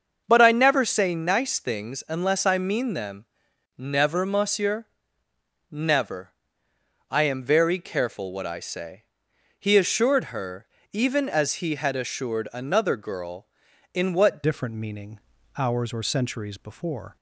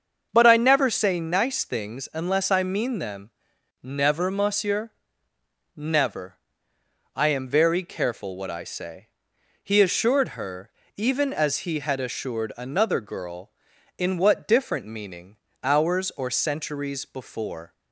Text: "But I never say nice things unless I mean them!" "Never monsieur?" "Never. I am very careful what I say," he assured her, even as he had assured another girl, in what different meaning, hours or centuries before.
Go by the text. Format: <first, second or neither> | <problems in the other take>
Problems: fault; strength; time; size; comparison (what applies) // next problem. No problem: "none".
second | starts louder than the rest; until 1.2 s; 6.5 dB; also in the second // changes voice at "different"; from 14.4 s on; 2.7 s long